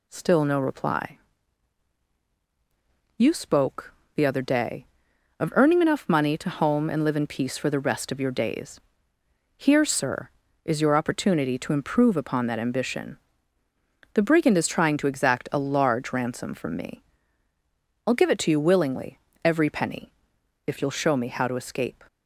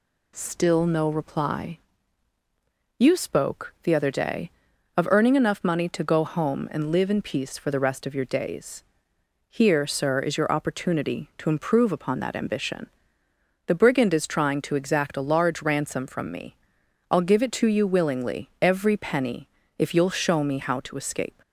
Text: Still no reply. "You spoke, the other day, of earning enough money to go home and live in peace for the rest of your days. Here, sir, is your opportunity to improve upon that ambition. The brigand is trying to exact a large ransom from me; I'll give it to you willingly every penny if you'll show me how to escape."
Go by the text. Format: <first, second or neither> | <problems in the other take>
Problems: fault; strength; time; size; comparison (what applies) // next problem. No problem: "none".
second | skips "go"; at 6.4 s // pauses between "willingly" and "every"; slight; at 19.1 s; 0.24 s long // pauses between "penny" and "if"; noticeable; at 20.1 s; 0.52 s long; slight in the second